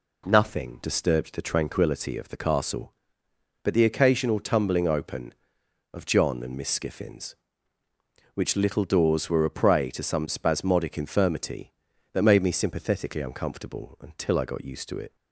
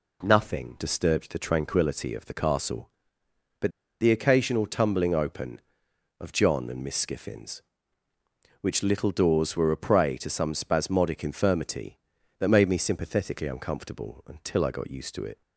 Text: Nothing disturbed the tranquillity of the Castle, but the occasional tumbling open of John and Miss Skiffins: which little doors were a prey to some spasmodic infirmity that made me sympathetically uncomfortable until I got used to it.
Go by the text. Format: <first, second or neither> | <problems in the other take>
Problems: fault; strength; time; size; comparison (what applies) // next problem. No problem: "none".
first | pauses between "but" and "the"; slight; at 3.7 s; 0.30 s long